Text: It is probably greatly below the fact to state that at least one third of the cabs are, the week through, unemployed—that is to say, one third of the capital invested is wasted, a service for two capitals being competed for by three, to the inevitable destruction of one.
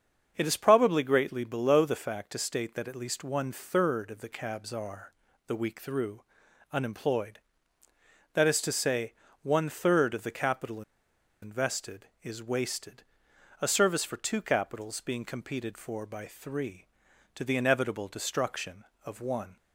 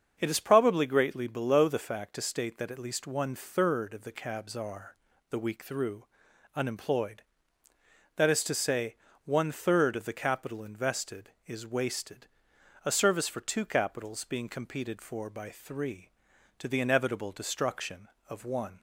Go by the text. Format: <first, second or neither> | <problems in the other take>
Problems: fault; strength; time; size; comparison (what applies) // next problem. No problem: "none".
second | starts louder than the rest; until 1.3 s; 7 dB; also in the second // pauses between "capital" and "invested"; noticeable; at 10.8 s; 0.59 s long